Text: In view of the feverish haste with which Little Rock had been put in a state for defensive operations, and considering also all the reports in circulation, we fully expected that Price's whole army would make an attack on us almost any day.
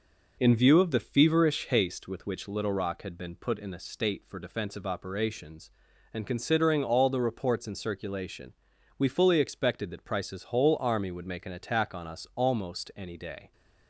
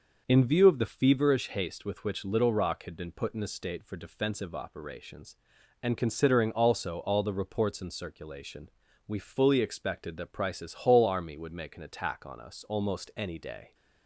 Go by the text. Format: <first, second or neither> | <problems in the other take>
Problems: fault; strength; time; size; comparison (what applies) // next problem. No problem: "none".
second | skips "also"; at 6.8 s